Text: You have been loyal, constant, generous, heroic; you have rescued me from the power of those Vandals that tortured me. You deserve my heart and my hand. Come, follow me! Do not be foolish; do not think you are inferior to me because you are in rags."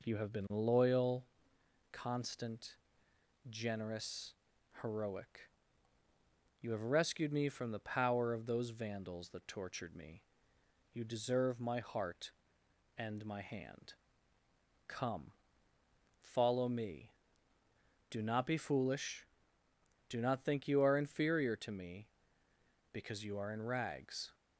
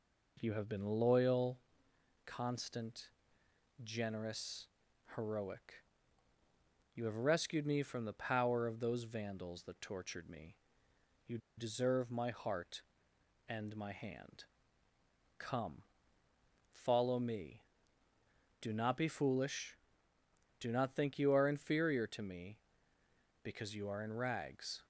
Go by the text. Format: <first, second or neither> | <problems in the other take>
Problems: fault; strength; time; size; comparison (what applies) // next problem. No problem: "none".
first | pauses between "You" and "deserve"; slight; at 11.3 s; 0.19 s long